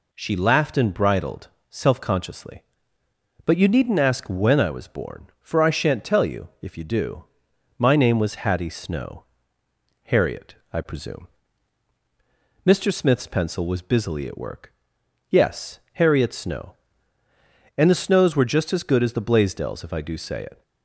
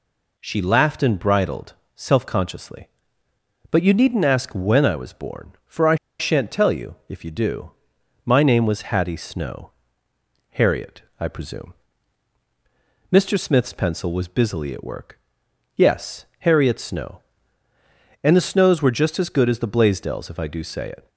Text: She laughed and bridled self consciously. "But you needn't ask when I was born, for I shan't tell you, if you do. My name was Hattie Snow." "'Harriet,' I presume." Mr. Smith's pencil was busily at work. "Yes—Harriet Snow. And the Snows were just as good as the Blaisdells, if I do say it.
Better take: first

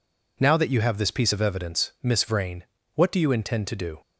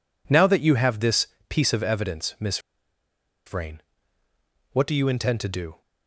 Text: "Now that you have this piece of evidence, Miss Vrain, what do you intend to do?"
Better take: first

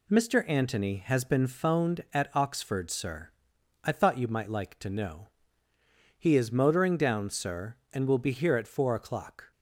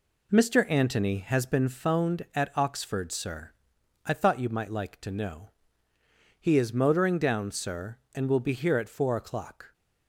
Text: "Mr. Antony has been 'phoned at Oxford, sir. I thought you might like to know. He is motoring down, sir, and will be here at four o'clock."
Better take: first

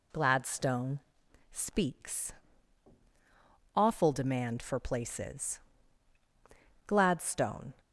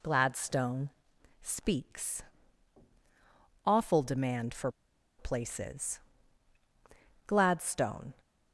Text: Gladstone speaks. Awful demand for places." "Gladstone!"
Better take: first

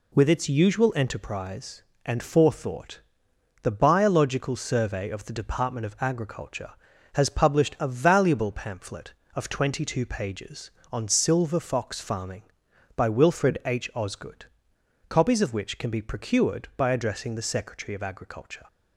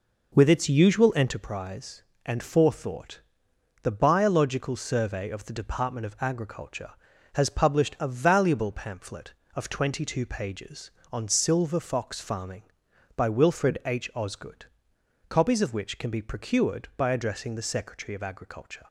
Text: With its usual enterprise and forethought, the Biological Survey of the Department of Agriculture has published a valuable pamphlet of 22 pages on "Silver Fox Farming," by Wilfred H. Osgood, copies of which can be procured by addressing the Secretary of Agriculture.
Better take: first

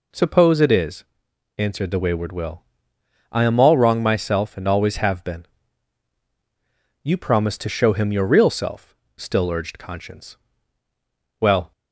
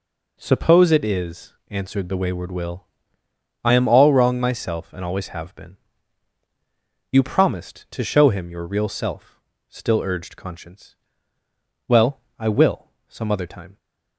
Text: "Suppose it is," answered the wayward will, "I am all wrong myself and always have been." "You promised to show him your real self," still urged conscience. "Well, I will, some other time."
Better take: second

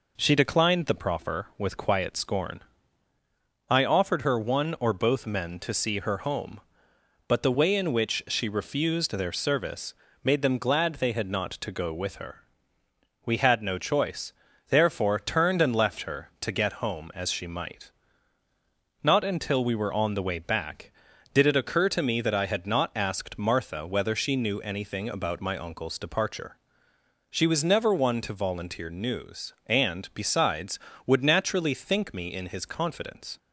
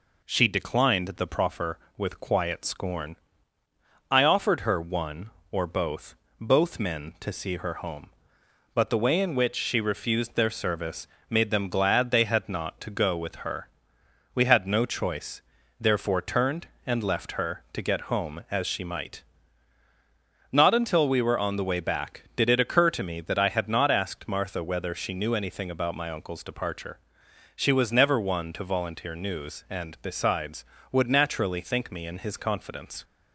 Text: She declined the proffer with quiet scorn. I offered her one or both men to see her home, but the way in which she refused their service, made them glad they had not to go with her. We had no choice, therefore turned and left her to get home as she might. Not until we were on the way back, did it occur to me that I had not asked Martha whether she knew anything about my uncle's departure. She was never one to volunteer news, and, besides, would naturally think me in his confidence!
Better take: first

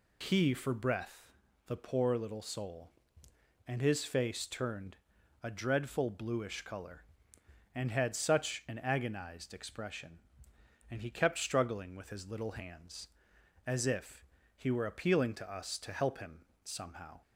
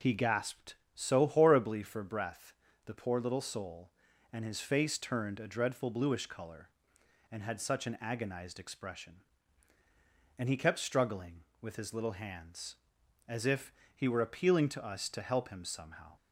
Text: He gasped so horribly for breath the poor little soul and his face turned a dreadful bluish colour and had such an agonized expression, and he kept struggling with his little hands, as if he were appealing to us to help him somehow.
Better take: second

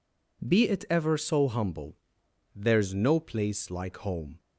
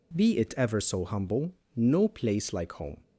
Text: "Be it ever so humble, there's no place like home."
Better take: first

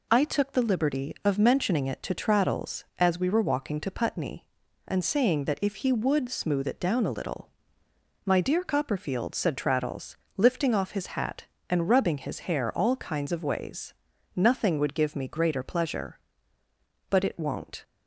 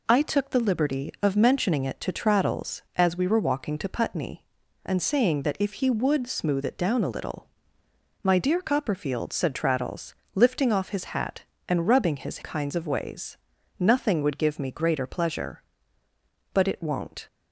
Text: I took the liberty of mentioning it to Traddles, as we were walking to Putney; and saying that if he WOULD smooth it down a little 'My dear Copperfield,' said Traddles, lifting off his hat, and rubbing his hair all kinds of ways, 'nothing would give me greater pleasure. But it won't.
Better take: first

